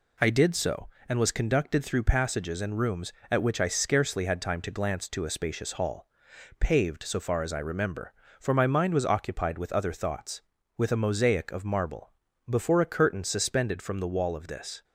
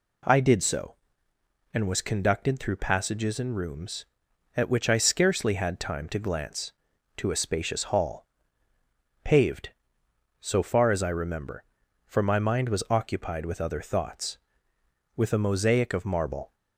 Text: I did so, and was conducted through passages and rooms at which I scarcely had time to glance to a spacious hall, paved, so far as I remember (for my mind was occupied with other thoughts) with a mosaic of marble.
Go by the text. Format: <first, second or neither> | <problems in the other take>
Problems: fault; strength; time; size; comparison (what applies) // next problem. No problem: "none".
second | goes on to say "Before a curtain suspended from the wall of this"; strong; from 12.4 s on; 2.3 s long